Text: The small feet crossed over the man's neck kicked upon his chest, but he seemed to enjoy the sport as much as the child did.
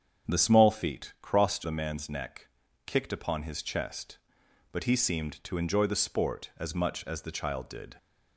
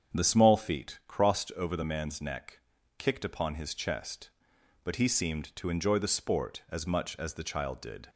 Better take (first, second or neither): second